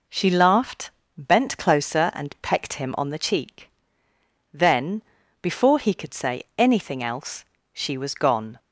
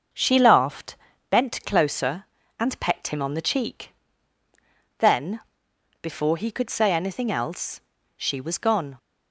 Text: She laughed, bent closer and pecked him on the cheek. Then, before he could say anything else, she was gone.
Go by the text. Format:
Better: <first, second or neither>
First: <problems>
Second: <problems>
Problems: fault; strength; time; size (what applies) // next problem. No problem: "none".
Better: first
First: none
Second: starts louder than the rest; noticeable; until 1.3 s; 6 dB